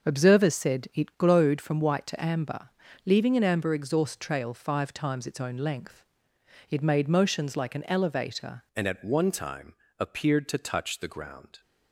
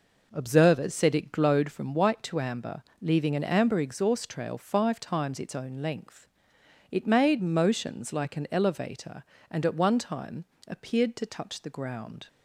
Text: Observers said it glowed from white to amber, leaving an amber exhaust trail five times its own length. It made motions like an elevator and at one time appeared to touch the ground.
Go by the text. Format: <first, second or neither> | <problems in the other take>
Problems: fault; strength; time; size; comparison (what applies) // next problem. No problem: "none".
second | changes voice at "and"; from 8.7 s on; 2.9 s long // pauses between "time" and "appeared"; slight; at 9.7 s; 0.24 s long; slight in the second